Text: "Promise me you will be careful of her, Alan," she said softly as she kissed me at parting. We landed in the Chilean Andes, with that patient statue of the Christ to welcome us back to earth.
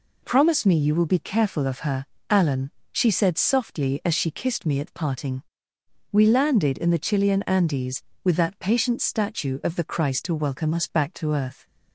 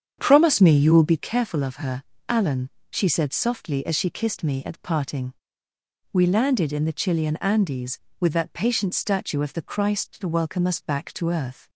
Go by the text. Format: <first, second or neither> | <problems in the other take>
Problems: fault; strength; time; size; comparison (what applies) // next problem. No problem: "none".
first | starts louder than the rest; strong; until 1.2 s; 8 dB